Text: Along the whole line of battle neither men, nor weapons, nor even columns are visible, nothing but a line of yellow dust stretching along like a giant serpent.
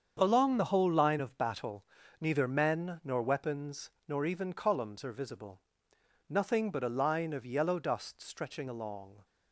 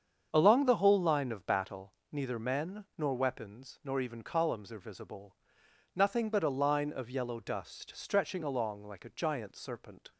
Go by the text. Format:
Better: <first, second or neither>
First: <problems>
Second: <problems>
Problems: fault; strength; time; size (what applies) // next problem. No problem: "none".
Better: second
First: starts louder than the rest; strong; until 1.2 s; 7.5 dB // pauses between "battle" and "neither"; at 1.8 s; 0.38 s long // stops before "like a giant serpent"; at 9.2 s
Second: starts louder than the rest; strong; until 1.3 s; 7.5 dB // pauses between "battle" and "neither"; slight; at 1.9 s; 0.20 s long